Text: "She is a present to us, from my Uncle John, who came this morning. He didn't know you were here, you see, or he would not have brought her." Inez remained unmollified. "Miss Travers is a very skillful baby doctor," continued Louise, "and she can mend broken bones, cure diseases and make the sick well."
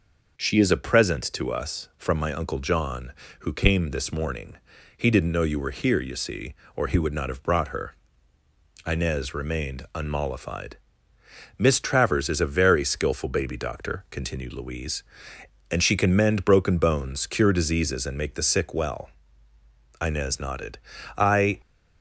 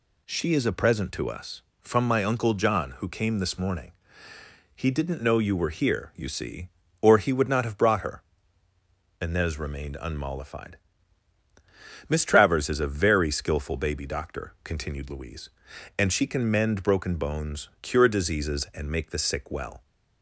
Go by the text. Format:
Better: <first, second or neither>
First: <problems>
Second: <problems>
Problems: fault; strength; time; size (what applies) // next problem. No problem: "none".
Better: second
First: goes on to say "Inez nodded I"; from 20.0 s on; 1.6 s long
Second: none